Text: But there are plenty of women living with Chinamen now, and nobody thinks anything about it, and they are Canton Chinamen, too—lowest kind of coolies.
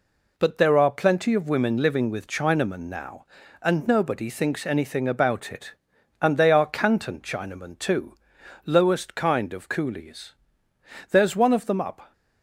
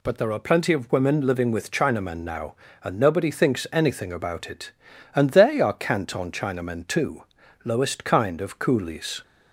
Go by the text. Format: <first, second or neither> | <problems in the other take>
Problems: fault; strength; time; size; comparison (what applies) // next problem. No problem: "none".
second | goes on to say "There's one of them up"; noticeable; from 11.1 s on; 1.0 s long